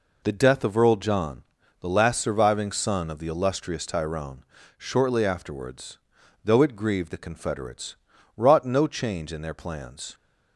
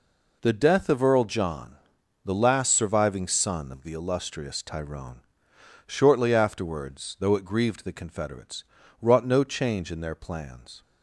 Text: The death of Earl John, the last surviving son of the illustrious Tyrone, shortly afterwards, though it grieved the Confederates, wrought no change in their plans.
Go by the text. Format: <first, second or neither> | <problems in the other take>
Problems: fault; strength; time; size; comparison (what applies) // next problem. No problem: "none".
neither | none